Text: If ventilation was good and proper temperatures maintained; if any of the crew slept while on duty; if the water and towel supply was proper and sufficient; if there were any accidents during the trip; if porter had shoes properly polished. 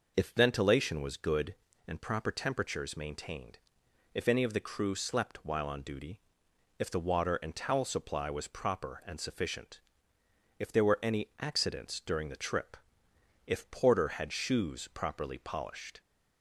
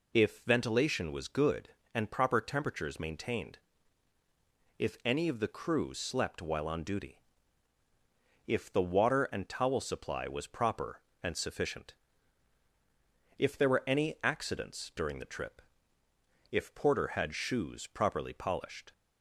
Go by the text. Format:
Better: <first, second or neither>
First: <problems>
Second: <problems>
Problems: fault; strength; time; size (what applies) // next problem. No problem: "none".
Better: neither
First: none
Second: none